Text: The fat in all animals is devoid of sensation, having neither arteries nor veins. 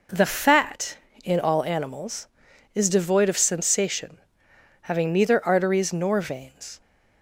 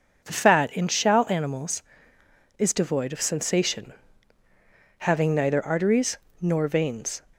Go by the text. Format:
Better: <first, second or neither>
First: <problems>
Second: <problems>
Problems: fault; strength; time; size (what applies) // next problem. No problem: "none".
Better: first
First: none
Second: says "shall" for "all"; at 0.8 s // pauses between "arteries" and "nor"; slight; at 6.1 s; 0.24 s long